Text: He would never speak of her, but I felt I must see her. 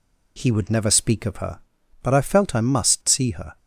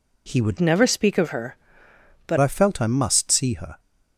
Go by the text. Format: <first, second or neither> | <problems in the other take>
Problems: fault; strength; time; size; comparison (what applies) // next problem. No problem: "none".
first | changes voice from "never" to "but"; from 0.6 to 2.3 s; 1.7 s long